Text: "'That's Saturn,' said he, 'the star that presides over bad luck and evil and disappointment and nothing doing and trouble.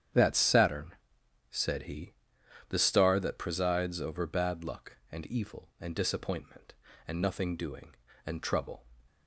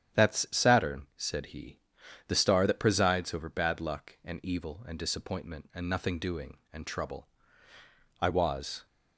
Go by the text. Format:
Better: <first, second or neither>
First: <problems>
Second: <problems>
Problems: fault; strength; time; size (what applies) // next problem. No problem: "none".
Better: first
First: starts louder than the rest; strong; until 1.6 s; 9.5 dB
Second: starts louder than the rest; strong; until 1.3 s; 9.5 dB // goes on to say "I was"; noticeable; from 8.2 s on; 0.64 s long